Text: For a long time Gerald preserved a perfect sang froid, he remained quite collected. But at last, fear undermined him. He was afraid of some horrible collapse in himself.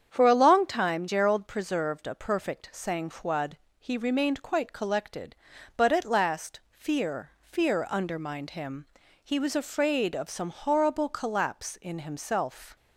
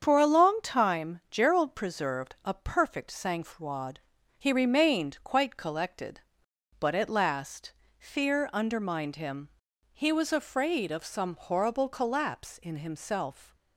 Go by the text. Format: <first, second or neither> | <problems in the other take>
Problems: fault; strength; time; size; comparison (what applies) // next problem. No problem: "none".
second | starts louder than the rest; strong; until 1.1 s; 8 dB; strong in the second // says "fear" twice; at 7.4 s